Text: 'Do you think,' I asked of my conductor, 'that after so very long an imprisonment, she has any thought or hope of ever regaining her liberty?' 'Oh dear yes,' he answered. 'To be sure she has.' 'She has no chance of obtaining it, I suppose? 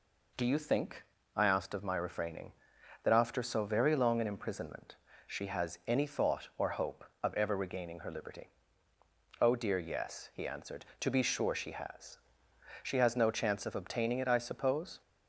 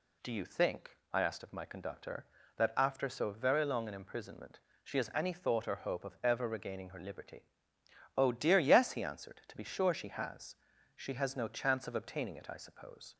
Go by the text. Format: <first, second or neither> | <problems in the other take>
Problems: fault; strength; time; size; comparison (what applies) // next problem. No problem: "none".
second | says "refraining" for "conductor"; at 1.9 s